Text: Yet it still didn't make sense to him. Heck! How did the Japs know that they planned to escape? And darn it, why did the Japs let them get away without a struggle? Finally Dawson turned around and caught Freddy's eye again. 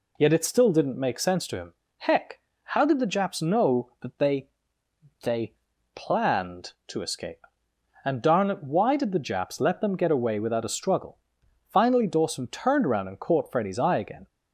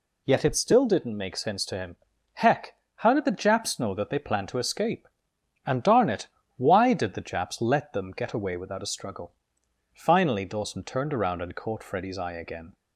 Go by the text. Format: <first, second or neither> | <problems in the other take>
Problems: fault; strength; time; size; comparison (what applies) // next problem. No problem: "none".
second | says "they" twice; at 5.2 s